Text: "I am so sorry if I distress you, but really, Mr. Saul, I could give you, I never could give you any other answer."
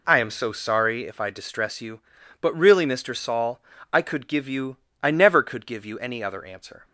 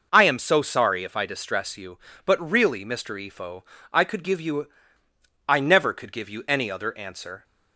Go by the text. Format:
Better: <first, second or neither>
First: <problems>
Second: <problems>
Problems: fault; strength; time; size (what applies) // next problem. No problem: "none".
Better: first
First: none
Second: says "Ifo" for "Saul"; at 3.1 s